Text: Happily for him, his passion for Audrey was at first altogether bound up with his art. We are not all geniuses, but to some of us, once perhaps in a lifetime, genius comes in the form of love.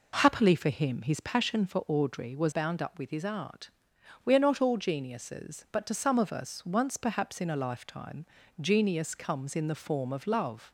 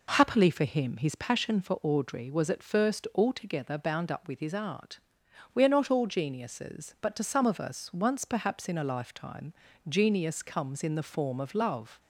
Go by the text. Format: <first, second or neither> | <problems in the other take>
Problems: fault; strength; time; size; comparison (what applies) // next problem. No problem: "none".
second | skips "at first altogether"; at 2.5 s